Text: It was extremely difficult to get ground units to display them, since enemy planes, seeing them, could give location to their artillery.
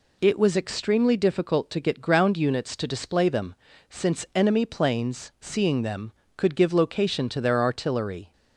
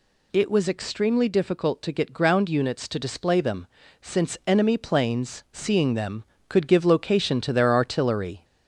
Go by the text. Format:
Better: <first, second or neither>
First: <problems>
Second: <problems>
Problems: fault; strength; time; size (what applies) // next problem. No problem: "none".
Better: first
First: none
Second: gets louder; slight; throughout; 2.5 dB